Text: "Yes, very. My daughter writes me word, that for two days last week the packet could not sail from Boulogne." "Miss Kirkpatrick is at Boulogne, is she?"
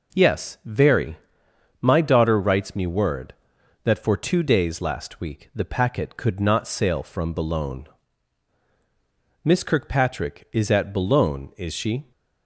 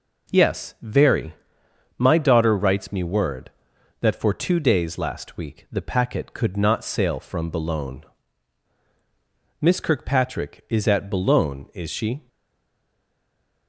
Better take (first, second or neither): first